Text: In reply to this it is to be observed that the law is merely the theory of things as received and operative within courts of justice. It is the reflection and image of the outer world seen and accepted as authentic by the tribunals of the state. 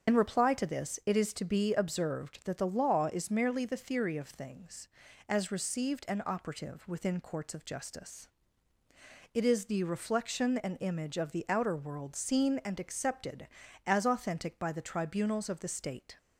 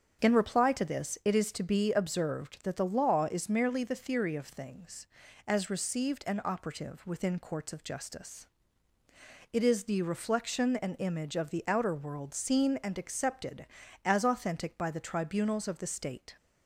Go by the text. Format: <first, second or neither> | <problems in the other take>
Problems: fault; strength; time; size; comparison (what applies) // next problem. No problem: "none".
second | loses the start of "In"; at 0.0 s; 65 ms // starts louder than the rest; until 1.1 s; 7 dB; strong in the second